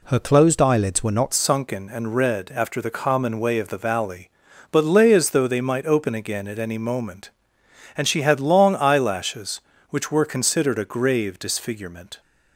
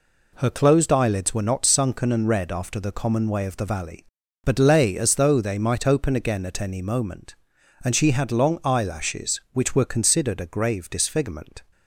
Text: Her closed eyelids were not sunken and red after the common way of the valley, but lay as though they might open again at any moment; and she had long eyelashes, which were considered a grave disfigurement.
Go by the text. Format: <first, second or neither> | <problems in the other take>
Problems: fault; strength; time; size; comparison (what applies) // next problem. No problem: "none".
second | changes voice at "sunken"; from 1.3 s on; 10.9 s long